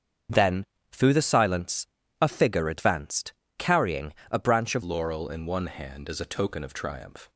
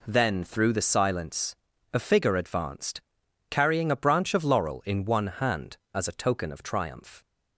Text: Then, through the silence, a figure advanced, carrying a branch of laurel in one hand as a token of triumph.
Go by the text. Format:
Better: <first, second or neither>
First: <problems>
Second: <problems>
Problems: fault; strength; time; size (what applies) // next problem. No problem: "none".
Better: second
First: starts louder than the rest; strong; until 1.6 s; 7.5 dB // pauses between "carrying" and "a"; slight; at 4.1 s; 0.18 s long // changes voice at "laurel"; from 4.8 s on; 2.4 s long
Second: none